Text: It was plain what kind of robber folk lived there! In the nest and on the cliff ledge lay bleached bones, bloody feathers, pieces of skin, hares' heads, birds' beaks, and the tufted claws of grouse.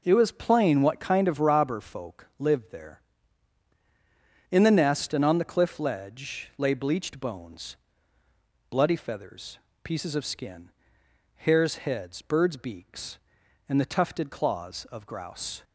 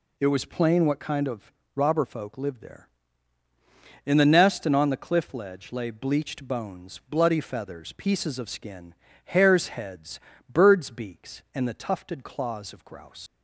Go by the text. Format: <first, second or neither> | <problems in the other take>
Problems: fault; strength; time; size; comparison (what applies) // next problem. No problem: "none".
first | pauses between "of" and "robber"; slight; at 1.5 s; 0.24 s long // leaves "grouse" unfinished; at 13.2 s; 130 ms